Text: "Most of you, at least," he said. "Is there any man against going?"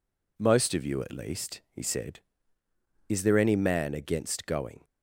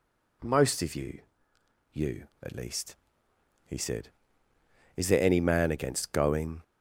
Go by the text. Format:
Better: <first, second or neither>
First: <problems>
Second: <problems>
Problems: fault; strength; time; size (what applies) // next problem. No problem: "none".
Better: first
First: none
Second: says "you" twice; at 1.9 s